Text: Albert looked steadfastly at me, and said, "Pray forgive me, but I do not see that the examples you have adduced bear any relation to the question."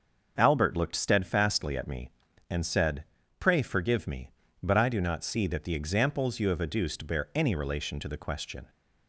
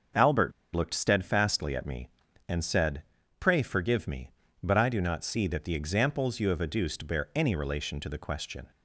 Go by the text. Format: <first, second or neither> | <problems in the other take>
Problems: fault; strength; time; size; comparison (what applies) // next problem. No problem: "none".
first | starts louder than the rest; until 1.3 s; 6.5 dB; also in the first // pauses between "Albert" and "looked"; slight; at 0.5 s; 0.23 s long